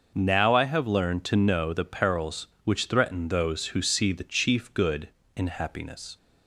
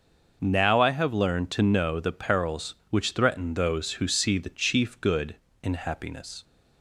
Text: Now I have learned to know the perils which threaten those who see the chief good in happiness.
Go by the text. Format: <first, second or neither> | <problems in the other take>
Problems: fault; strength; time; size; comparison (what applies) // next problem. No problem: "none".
neither | none